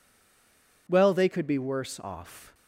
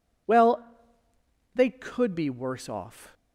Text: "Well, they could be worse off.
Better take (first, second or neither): second